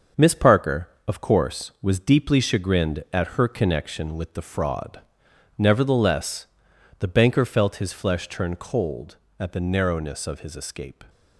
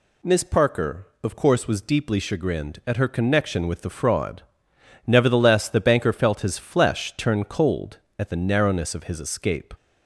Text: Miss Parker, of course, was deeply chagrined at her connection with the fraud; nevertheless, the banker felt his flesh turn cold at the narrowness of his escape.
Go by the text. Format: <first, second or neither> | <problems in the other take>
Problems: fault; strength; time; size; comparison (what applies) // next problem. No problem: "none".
second | gets quieter; throughout; 6.5 dB